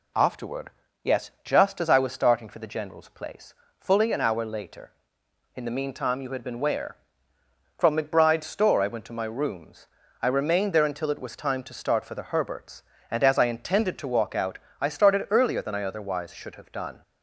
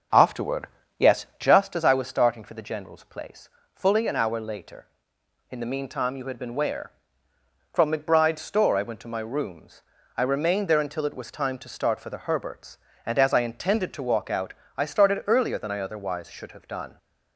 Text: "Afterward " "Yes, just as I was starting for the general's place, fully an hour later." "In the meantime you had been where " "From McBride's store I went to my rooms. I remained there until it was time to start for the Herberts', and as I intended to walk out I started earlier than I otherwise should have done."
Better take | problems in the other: first | starts louder than the rest; noticeable; until 1.6 s; 6 dB // pauses between "out" and "I"; slight; at 14.5 s; 0.24 s long; slight in the first

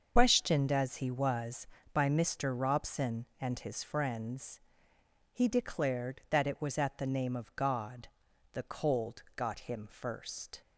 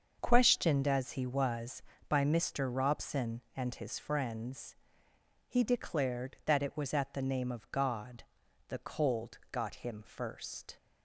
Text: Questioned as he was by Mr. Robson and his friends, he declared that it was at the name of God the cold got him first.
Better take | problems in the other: second | loses the start of "Questioned"; at 0.1 s; 110 ms // starts louder than the rest; until 1.1 s; 6.5 dB; also in the second // pauses between "God" and "the"; at 8.0 s; 0.44 s long; also in the second

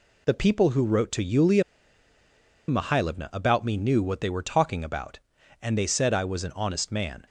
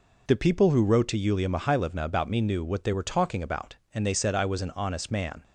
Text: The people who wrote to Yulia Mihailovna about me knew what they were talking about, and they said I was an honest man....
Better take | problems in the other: second | pauses between "Yulia" and "Mihailovna"; at 1.6 s; 1.0 s long

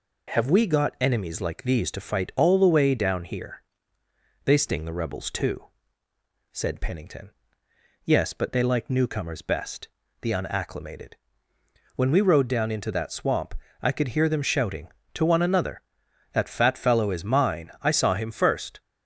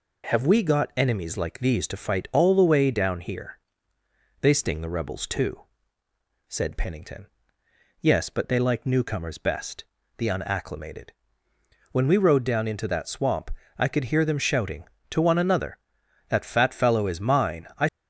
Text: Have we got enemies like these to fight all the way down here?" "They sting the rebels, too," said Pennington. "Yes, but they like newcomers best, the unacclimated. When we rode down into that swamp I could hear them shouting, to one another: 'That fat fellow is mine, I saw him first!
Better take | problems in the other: first | pauses between "swamp" and "I"; slight; at 13.5 s; 0.26 s long; slight in the first // stops before "saw him first"; at 17.8 s

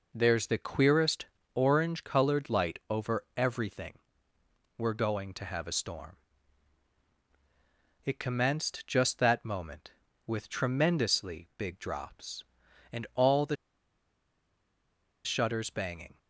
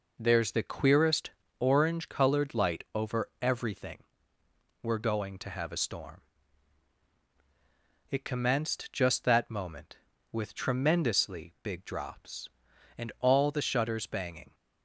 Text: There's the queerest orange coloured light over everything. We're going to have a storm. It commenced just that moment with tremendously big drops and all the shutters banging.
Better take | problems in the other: second | pauses between "queerest" and "orange"; slight; at 1.2 s; 0.28 s long; slight in the second // pauses between "the" and "shutters"; strong; at 13.5 s; 1.6 s long

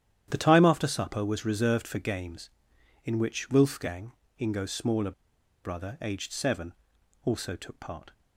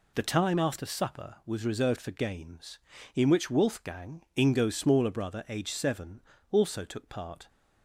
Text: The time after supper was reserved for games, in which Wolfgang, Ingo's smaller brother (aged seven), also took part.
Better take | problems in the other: second | starts louder than the rest; strong; until 1.2 s; 10.5 dB // pauses between "smaller" and "brother"; noticeable; at 5.1 s; 0.52 s long

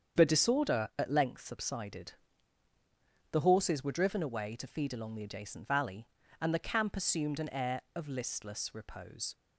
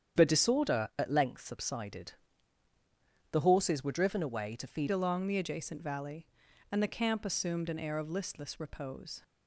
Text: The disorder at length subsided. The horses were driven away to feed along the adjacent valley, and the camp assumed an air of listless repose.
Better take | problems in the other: first | starts louder than the rest; strong; until 1.2 s; 8.5 dB; strong in the first // changes voice at "along"; from 4.8 s on; 4.4 s long

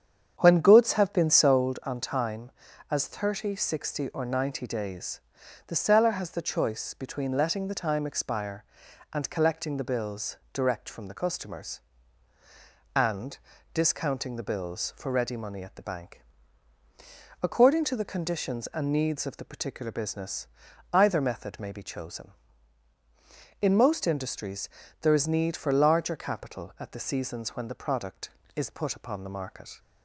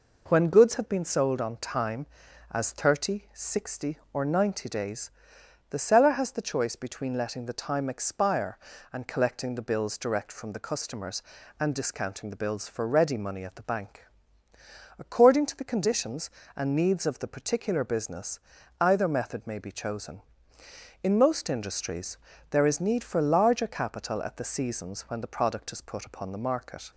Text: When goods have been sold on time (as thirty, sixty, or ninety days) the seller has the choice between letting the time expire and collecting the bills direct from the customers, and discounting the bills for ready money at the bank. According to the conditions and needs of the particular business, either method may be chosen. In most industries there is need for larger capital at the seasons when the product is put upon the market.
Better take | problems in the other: second | starts louder than the rest; strong; until 1.6 s; 8 dB // pauses between "bills" and "direct"; slight; at 10.3 s; 0.18 s long // pauses between "and" and "discounting"; slight; at 13.3 s; 0.34 s long // pauses between "industries" and "there"; slight; at 24.6 s; 0.34 s long; slight in the second

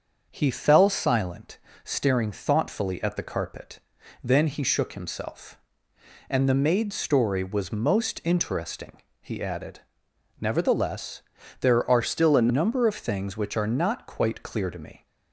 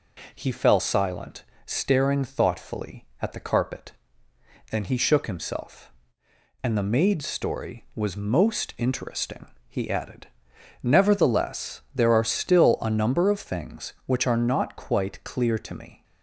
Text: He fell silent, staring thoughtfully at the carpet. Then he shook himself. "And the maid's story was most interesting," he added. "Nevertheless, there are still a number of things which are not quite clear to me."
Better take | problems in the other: second | starts louder than the rest; until 1.3 s; 7 dB // changes voice from "still" to "a"; from 12.0 to 12.4 s; 0.4 s long

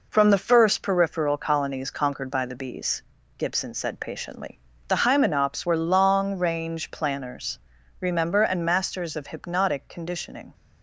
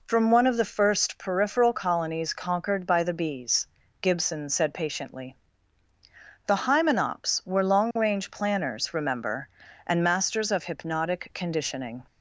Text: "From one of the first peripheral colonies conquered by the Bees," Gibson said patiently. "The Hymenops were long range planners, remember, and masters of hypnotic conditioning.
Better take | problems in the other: second | skips "one of"; at 0.3 s

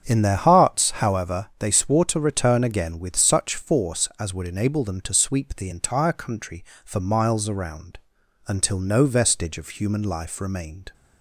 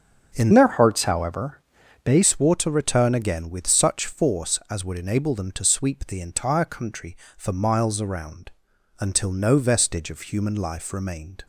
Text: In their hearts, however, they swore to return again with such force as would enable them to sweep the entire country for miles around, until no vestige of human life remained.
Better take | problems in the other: first | starts louder than the rest; strong; until 1.3 s; 7 dB; strong in the first // changes voice from "their" to "they"; from 0.5 to 2.2 s; 1.7 s long

